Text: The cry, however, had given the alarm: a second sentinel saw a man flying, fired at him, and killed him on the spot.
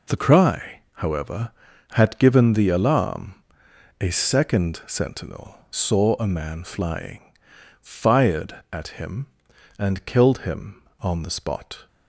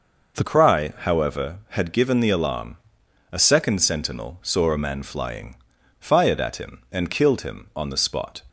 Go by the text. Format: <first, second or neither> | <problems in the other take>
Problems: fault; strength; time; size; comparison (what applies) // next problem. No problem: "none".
first | changes voice at "cry"; from 0.4 s on; 8.0 s long